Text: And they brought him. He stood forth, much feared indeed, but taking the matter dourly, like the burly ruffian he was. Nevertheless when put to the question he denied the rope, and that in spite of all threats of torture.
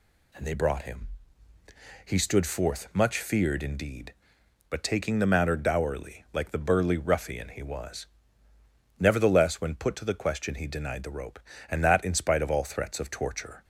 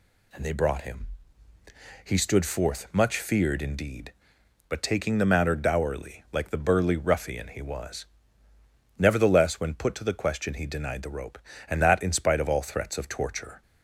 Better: neither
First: none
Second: none

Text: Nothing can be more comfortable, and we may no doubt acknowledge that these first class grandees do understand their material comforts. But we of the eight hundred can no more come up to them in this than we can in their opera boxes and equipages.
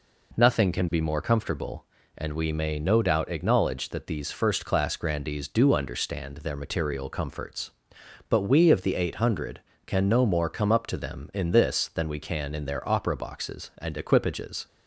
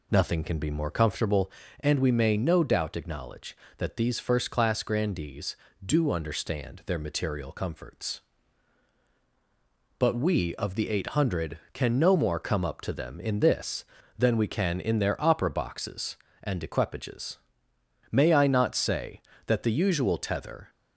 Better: first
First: none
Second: goes on to say "May I not say that the usual tether"; strong; from 18.0 s on; 2.6 s long

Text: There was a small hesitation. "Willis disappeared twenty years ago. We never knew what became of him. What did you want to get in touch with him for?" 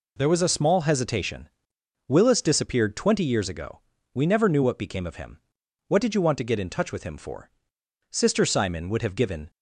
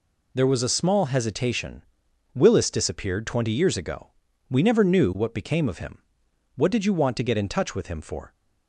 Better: second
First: goes on to say "Sister Simon would have given"; from 8.1 s on; 1.3 s long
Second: none

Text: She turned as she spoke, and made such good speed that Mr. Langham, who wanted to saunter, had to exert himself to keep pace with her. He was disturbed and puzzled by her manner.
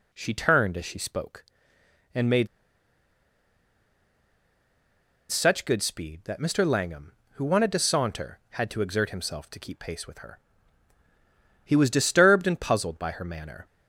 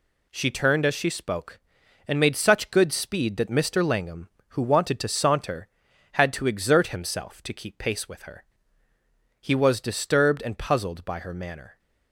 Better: second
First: pauses between "made" and "such"; strong; at 2.4 s; 2.8 s long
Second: none

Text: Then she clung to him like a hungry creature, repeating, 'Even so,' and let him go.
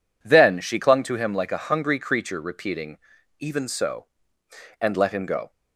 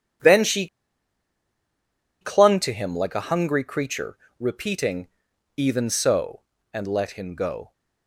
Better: first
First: none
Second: pauses between "she" and "clung"; strong; at 0.6 s; 1.5 s long

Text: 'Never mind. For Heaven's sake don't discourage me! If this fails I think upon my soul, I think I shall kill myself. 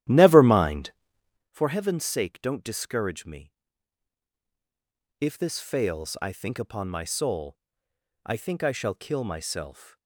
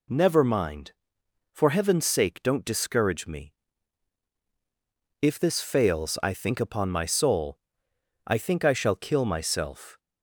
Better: second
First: starts louder than the rest; strong; until 1.6 s; 12.5 dB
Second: none

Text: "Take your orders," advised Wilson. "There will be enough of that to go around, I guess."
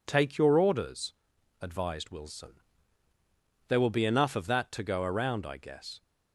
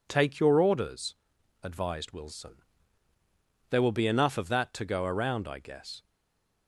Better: first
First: none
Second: stays silent after the last word; slight; from 6.0 s on; 0.6 s long

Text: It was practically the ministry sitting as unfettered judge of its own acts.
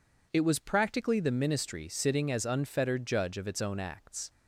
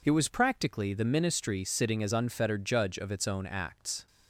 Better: neither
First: none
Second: none

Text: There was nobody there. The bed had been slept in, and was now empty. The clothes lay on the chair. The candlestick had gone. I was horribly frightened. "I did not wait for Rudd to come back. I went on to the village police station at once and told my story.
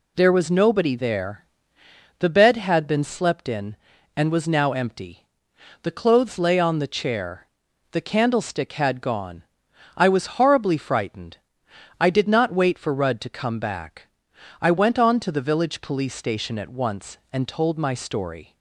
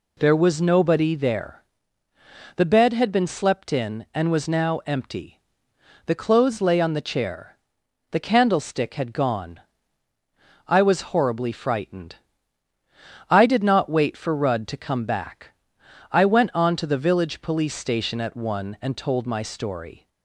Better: first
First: none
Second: says "one" for "once"; at 18.3 s

